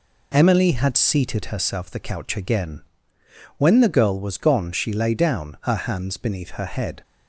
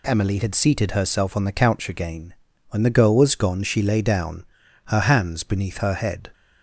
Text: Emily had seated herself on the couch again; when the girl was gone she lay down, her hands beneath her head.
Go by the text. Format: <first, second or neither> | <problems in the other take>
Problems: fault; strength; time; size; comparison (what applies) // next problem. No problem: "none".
second | skips "on"; at 1.9 s